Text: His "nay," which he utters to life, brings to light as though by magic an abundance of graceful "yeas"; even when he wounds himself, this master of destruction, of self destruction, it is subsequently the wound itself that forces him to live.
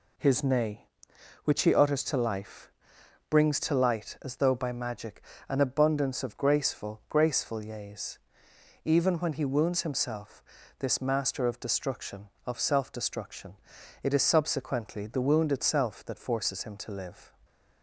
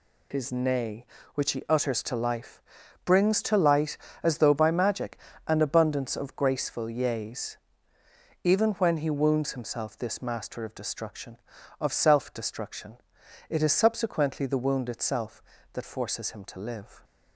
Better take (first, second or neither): second